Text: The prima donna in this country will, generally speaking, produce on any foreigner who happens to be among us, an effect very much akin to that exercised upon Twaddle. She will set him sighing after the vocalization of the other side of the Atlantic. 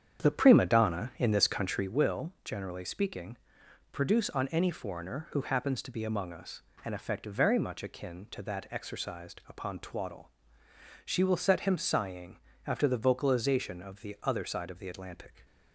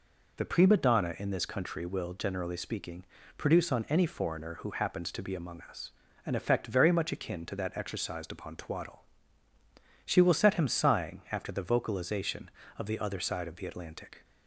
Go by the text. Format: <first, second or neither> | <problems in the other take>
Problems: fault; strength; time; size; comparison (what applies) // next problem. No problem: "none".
second | starts louder than the rest; strong; until 1.9 s; 8 dB // pauses between "sighing" and "after"; slight; at 12.3 s; 0.30 s long